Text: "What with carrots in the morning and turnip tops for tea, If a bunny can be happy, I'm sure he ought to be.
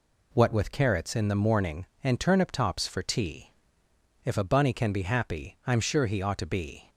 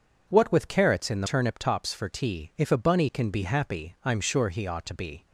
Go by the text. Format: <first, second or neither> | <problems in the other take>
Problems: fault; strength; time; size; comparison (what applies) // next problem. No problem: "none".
first | skips "morning and"; at 1.2 s